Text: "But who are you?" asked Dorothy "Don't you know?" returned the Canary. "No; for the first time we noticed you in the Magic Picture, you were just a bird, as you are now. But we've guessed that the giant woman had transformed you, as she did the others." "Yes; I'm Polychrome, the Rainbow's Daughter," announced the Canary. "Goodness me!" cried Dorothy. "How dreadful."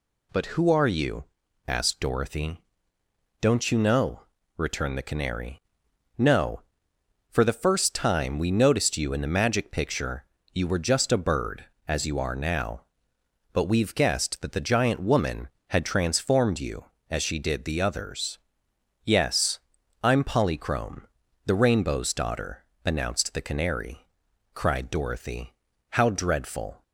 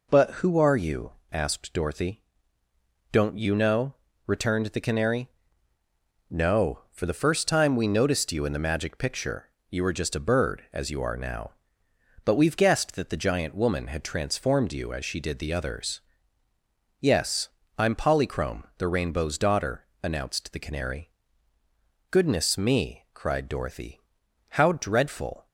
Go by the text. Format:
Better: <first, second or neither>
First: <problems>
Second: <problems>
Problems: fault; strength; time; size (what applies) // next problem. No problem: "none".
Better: second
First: pauses between "Dorothy" and "Don't"; noticeable; at 2.5 s; 0.82 s long // skips "Goodness me"; at 24.3 s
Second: pauses between "Dorothy" and "Don't"; noticeable; at 2.2 s; 0.90 s long